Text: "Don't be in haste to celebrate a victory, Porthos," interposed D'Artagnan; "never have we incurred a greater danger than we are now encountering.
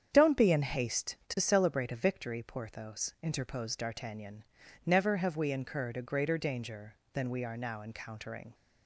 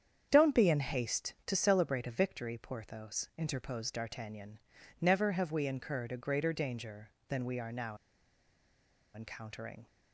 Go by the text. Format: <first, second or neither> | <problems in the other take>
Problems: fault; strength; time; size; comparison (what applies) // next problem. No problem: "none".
first | starts louder than the rest; strong; until 1.3 s; 8 dB; strong in the first // pauses between "now" and "encountering"; at 7.9 s; 1.1 s long